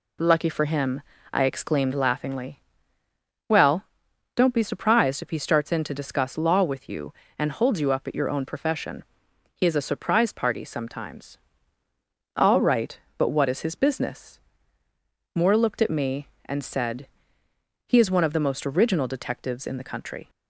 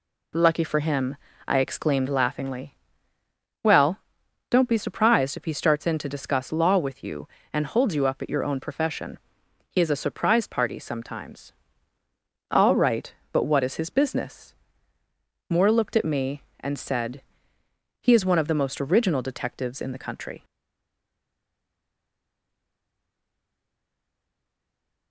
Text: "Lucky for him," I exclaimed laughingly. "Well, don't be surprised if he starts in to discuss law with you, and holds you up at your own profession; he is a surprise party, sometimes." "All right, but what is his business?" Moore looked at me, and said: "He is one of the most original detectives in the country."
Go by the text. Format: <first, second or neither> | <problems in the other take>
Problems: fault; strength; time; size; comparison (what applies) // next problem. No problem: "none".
first | stays silent after the last word; strong; from 20.4 s on; 4.7 s long